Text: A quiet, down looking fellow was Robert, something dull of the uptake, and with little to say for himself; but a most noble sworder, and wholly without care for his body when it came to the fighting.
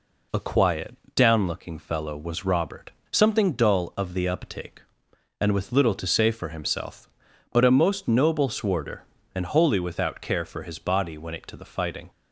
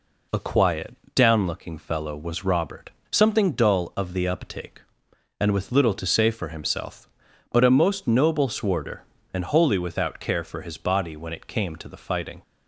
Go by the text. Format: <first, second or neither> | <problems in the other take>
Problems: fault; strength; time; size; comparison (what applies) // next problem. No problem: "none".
second | skips "came"; at 11.4 s